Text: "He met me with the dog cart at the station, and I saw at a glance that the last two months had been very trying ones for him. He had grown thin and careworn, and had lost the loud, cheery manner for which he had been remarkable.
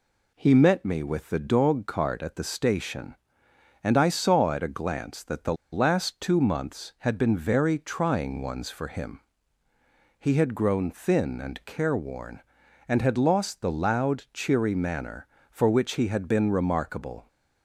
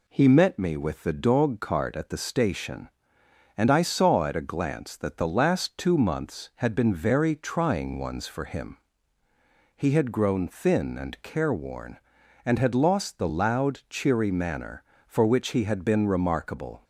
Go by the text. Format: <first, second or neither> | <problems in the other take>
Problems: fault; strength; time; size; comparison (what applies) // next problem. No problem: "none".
second | pauses between "the" and "last"; slight; at 5.5 s; 0.19 s long